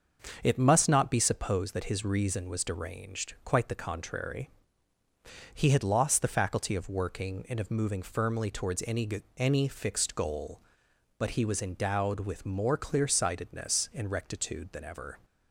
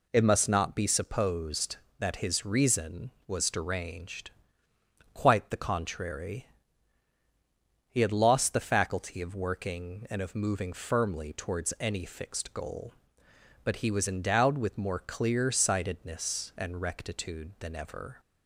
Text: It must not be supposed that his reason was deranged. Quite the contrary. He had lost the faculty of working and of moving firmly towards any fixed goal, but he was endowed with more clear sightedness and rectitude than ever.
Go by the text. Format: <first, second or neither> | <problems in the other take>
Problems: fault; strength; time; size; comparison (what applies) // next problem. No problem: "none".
second | starts louder than the rest; until 1.4 s; 6.5 dB // says "any" twice; at 9.3 s